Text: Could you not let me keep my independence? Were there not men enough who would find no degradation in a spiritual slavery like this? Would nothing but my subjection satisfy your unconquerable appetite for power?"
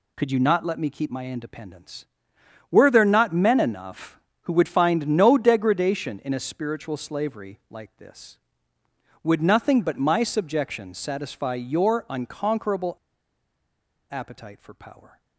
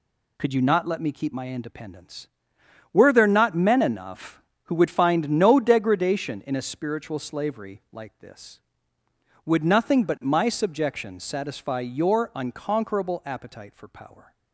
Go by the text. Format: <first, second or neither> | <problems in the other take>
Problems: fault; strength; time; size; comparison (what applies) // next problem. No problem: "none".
second | pauses between "unconquerable" and "appetite"; at 12.9 s; 1.1 s long